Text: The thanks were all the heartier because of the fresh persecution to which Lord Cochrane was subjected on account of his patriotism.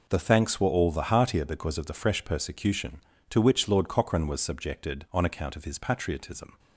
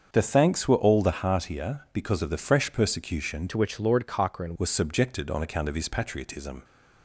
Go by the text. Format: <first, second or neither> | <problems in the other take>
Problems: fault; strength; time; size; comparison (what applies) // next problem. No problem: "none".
first | starts louder than the rest; until 1.1 s; 7 dB // changes voice from "to" to "Cochrane"; from 3.4 to 4.5 s; 1.1 s long